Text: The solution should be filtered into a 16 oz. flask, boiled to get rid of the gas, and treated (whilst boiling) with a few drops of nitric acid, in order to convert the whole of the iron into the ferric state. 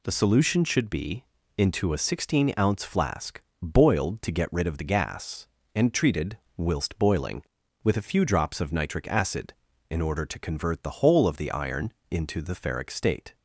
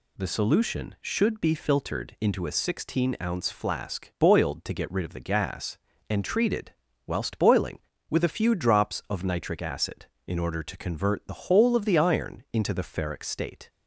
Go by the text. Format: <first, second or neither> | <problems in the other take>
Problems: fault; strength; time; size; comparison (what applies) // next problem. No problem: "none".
second | skips "filtered"; at 1.4 s // pauses between "iron" and "into"; slight; at 11.9 s; 0.16 s long